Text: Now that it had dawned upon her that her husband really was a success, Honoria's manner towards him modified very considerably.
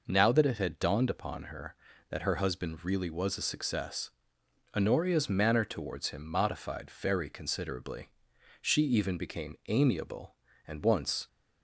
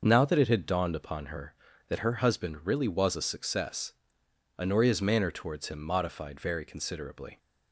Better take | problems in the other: second | goes on to say "She even became amiable and once"; strong; from 8.6 s on; 2.6 s long

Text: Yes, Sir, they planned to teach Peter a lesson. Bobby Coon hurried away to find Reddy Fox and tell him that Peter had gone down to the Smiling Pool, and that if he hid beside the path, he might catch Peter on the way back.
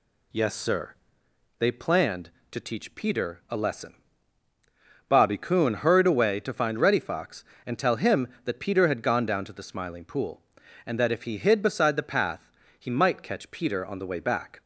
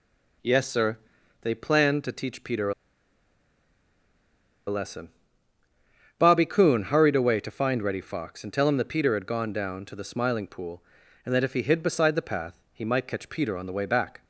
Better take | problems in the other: first | pauses between "a" and "lesson"; strong; at 2.7 s; 1.9 s long

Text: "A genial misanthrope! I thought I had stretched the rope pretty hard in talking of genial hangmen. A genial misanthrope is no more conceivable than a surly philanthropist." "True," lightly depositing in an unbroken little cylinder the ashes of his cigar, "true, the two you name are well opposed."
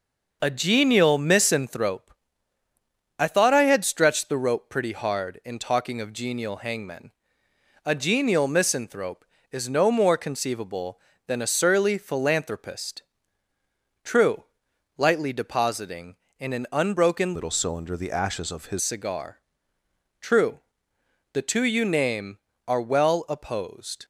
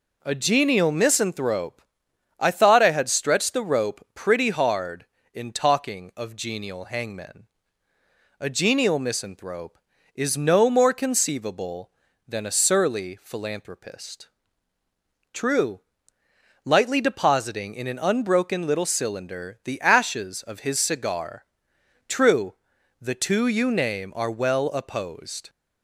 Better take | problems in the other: second | changes voice from "little" to "his"; from 17.3 to 18.8 s; 1.5 s long

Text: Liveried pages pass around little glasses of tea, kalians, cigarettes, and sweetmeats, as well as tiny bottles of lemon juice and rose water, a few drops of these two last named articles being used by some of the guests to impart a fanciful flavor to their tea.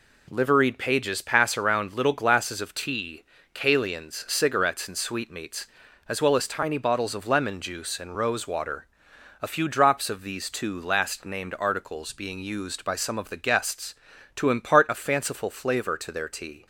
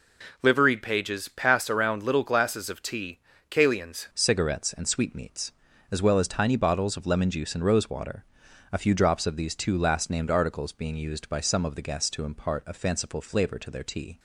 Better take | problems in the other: first | changes voice at "cigarettes"; from 4.1 s on; 10.0 s long

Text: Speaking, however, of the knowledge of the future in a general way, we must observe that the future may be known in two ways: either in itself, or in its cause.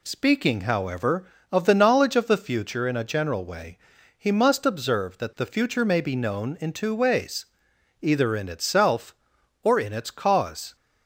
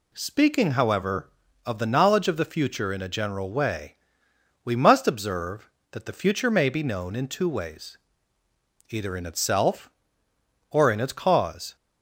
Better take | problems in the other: second | says "he" for "we"; at 4.1 s

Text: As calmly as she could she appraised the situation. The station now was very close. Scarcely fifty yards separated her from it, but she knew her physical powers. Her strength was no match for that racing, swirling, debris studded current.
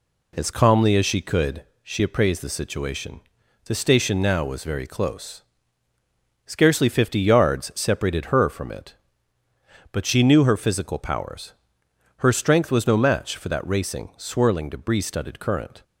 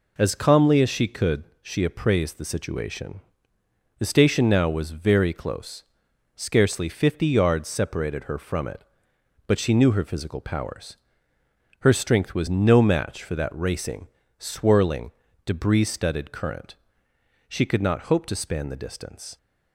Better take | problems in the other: first | pauses between "could" and "she"; slight; at 1.4 s; 0.18 s long; slight in the first // goes on to say "She could not hope to span the distance"; strong; from 17.4 s on; 1.8 s long

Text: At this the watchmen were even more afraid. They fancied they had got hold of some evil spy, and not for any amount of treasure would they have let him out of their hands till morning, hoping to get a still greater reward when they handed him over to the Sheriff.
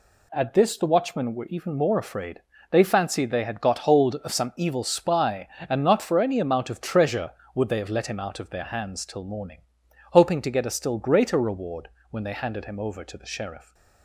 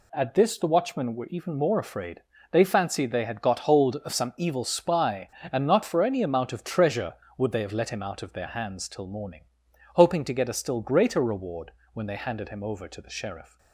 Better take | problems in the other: neither | pauses between "reward" and "when"; slight; the same in both

